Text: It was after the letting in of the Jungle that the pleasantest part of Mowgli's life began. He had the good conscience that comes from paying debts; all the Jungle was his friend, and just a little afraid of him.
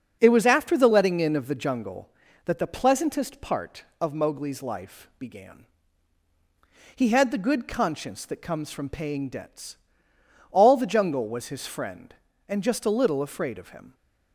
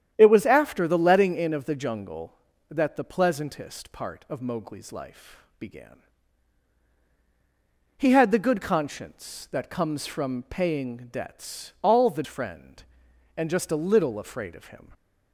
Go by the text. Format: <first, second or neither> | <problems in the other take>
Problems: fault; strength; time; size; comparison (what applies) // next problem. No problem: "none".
first | starts louder than the rest; strong; until 1.1 s; 9.5 dB; also in the first // pauses between "life" and "began"; slight; at 5.4 s; 0.16 s long // skips "Jungle was his"; at 12.2 s